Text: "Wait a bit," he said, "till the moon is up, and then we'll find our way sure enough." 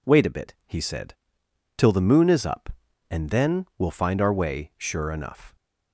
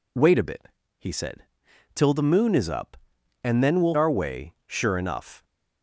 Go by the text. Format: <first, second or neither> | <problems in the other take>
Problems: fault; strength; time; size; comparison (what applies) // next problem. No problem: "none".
first | skips "find"; at 3.9 s